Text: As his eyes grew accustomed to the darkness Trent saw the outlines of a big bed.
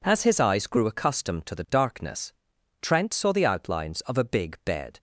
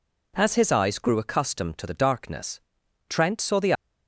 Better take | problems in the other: first | pauses between "darkness" and "Trent"; noticeable; at 2.5 s; 0.48 s long; noticeable in the first // stops before "outlines of a big bed"; at 3.7 s

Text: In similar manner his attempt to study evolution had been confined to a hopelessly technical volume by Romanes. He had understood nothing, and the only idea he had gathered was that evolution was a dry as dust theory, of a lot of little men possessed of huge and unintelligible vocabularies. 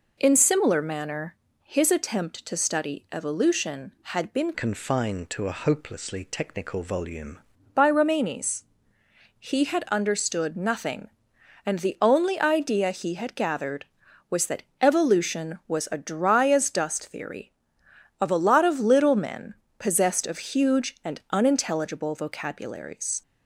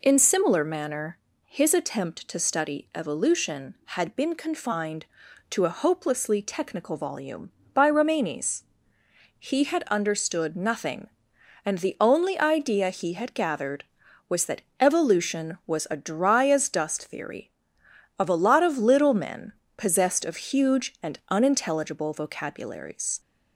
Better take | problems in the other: second | pauses between "manner" and "his"; slight; at 1.3 s; 0.28 s long; slight in the second // changes voice from "confined" to "volume"; from 4.5 to 7.3 s; 2.8 s long // pauses between "that" and "evolution"; slight; at 14.6 s; 0.16 s long; slight in the second // pauses between "men" and "possessed"; slight; at 19.5 s; 0.24 s long; slight in the second

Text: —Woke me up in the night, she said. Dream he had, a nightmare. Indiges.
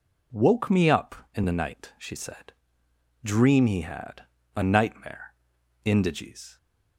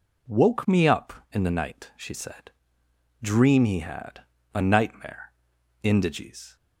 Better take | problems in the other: neither | none

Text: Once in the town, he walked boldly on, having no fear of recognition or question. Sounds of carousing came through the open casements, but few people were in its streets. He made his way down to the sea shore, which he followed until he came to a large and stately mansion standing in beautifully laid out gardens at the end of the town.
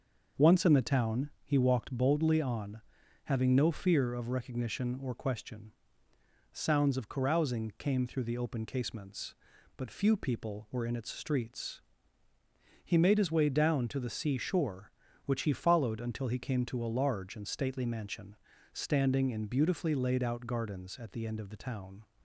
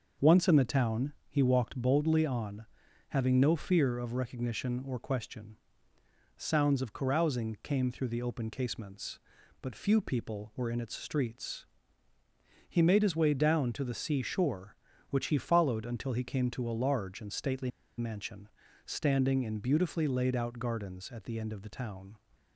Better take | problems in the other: first | pauses between "stately" and "mansion"; slight; at 17.7 s; 0.28 s long // pauses between "mansion" and "standing"; at 18.4 s; 0.40 s long; also in the first

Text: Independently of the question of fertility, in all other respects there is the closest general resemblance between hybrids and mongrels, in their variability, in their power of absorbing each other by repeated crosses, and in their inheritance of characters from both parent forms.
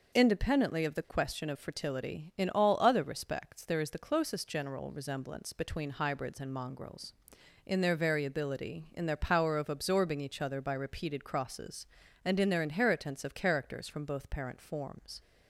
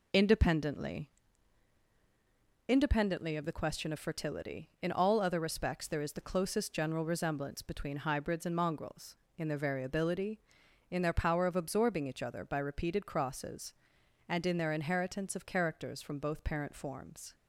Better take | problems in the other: first | says "Independently" twice; at 2.6 s

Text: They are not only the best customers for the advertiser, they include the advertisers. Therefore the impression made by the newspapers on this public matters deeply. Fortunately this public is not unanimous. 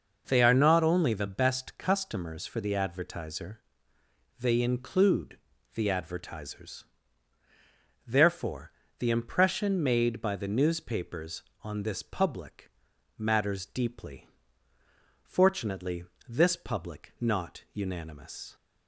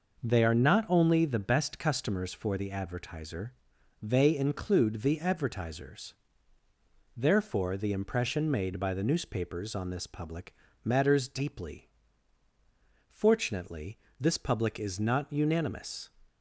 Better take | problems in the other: second | pauses between "include" and "the"; at 5.3 s; 0.38 s long // pauses between "Therefore" and "the"; slight; at 8.7 s; 0.28 s long // pauses between "public" and "matters"; noticeable; at 12.6 s; 0.48 s long; slight in the second // pauses between "Fortunately" and "this"; slight; at 16.0 s; 0.24 s long; slight in the second // skips "is"; at 17.1 s

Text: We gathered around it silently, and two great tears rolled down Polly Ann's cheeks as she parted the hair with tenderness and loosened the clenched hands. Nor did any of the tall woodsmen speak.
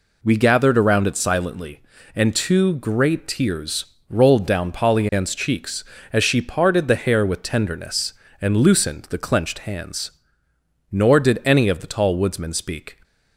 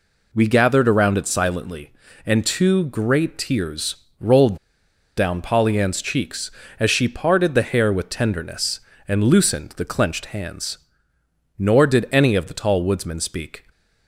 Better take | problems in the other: first | pauses between "tears" and "rolled"; slight; at 3.9 s; 0.24 s long; slight in the first // pauses between "rolled" and "down"; noticeable; at 4.5 s; 0.61 s long

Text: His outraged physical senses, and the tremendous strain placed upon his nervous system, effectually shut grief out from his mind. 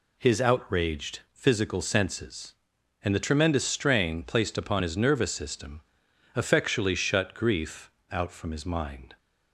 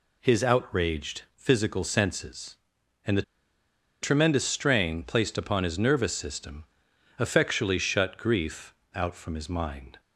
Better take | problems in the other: first | pauses between "the" and "tremendous"; noticeable; at 3.2 s; 0.79 s long // pauses between "grief" and "out"; slight; at 8.7 s; 0.22 s long; slight in the first

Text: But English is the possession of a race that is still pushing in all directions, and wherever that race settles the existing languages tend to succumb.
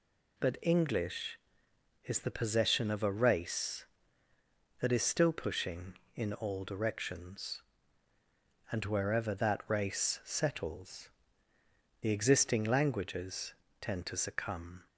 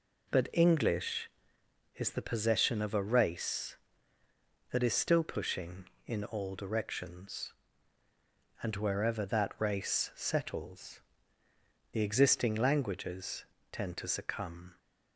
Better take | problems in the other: first | starts louder than the rest; until 1.6 s; 3.5 dB // pauses between "settles" and "the"; noticeable; at 10.9 s; 0.92 s long; noticeable in the first // pauses between "languages" and "tend"; slight; at 13.4 s; 0.26 s long; slight in the first

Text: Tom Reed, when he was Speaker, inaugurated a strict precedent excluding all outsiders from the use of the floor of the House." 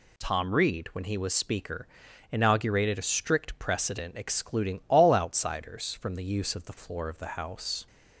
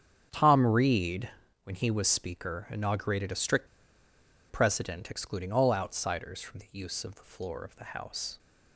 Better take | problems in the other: first | starts louder than the rest; strong; until 1.6 s; 8 dB // pauses between "strict" and "precedent"; noticeable; at 3.6 s; 0.82 s long

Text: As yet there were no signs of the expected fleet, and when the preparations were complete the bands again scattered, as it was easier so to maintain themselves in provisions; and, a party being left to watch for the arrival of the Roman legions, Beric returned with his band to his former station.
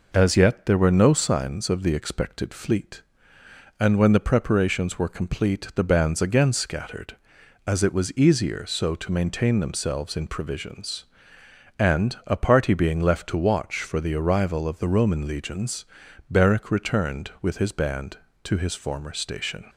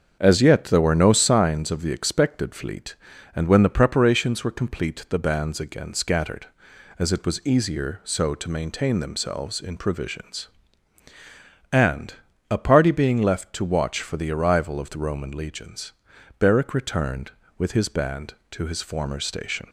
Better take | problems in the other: first | starts louder than the rest; strong; until 1.4 s; 7 dB

